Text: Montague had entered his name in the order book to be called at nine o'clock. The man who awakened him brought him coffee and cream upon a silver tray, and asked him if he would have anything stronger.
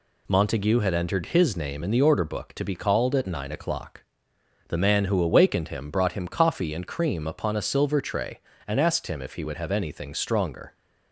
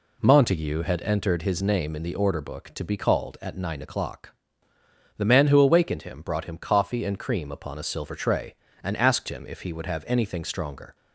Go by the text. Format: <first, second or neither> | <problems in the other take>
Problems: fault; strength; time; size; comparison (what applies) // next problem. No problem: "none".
neither | none